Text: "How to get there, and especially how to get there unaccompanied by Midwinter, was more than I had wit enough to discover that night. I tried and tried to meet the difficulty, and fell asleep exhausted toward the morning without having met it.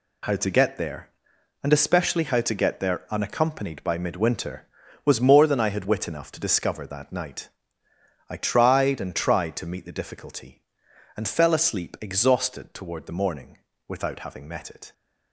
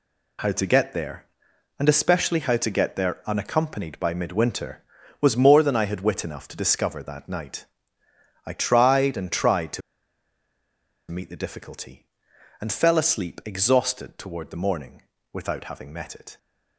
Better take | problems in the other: first | pauses between "to" and "meet"; strong; at 9.8 s; 1.2 s long // pauses between "morning" and "without"; slight; at 15.0 s; 0.32 s long; slight in the first

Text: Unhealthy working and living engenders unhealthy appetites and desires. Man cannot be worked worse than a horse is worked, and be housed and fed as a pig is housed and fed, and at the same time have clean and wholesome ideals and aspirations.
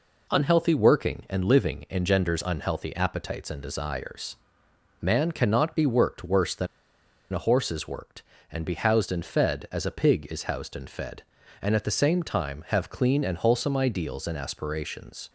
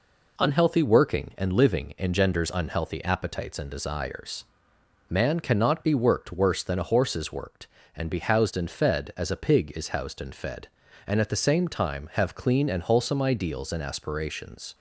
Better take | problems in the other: second | pauses between "than" and "a"; noticeable; at 6.6 s; 0.66 s long

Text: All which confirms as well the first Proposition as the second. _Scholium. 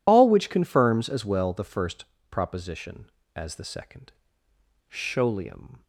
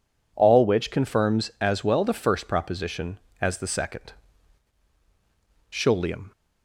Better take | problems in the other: second | loses the start of "All"; at 0.0 s; 45 ms // pauses between "first" and "Proposition"; slight; at 2.0 s; 0.24 s long

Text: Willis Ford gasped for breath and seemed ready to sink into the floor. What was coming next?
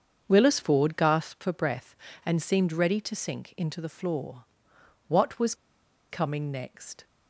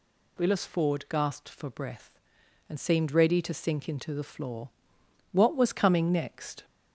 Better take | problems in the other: second | starts louder than the rest; until 1.2 s; 7 dB // pauses between "was" and "coming"; noticeable; at 5.5 s; 0.56 s long

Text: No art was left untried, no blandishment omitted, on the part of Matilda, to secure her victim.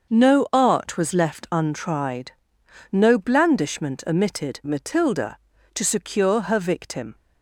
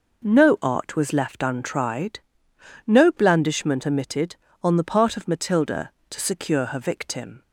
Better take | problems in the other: second | starts louder than the rest; until 1.1 s; 6.5 dB // skips "on the part of"; at 4.6 s

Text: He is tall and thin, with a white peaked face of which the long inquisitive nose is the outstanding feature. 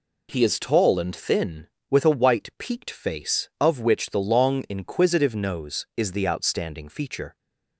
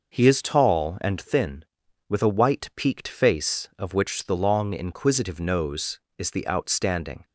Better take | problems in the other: first | stops before "feature"; at 7.2 s

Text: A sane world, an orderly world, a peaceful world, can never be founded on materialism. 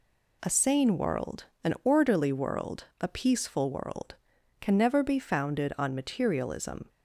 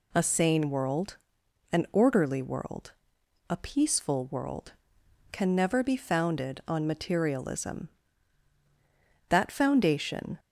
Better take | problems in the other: first | goes on to say "That foundation"; noticeable; from 9.2 s on; 1.1 s long

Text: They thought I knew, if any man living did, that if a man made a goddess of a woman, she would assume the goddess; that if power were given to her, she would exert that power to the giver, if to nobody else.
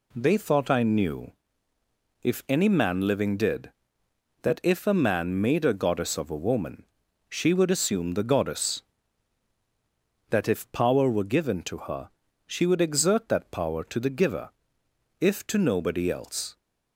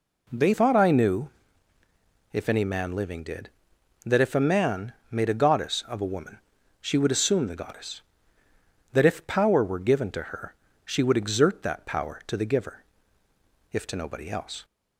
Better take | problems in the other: first | changes voice at "thought"; from 0.5 s on; 14.1 s long // pauses between "man" and "made"; slight; at 4.9 s; 0.16 s long

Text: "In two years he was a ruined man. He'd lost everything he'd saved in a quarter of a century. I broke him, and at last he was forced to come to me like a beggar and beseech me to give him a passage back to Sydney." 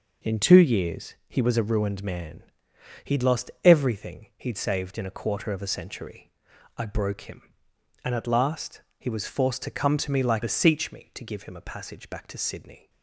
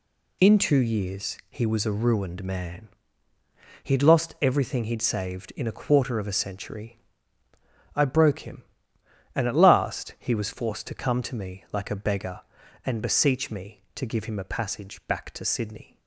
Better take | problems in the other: second | pauses between "last" and "he"; slight; at 8.8 s; 0.16 s long // skips "a beggar and"; at 10.4 s

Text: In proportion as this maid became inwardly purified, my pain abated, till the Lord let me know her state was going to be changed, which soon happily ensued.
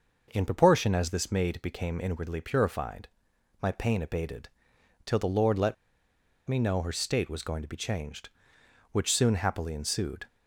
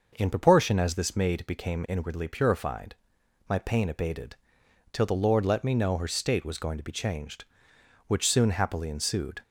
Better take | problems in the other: second | pauses between "let" and "me"; noticeable; at 5.7 s; 0.71 s long

